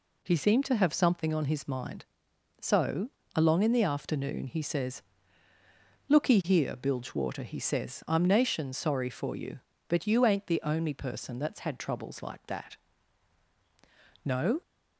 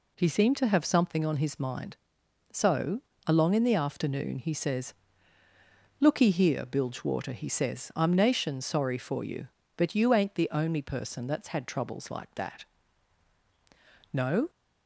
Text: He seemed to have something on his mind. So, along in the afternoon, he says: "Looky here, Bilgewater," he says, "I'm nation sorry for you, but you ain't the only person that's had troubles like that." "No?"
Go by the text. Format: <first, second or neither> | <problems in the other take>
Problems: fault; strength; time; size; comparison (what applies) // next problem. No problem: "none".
neither | none